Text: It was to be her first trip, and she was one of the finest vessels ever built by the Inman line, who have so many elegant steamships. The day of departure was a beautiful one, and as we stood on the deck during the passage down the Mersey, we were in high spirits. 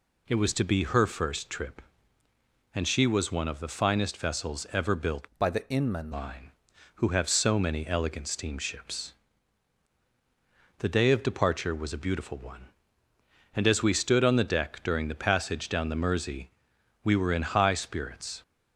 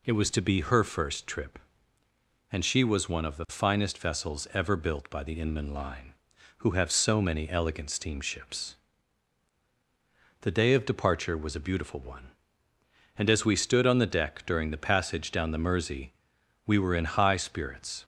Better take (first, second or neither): second